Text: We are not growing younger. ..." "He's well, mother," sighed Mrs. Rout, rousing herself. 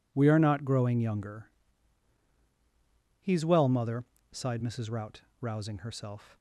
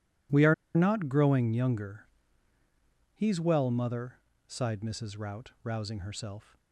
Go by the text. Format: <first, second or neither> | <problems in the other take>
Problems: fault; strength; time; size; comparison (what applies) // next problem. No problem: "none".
first | starts louder than the rest; strong; until 1.5 s; 12.5 dB // pauses between "are" and "not"; slight; at 0.5 s; 0.20 s long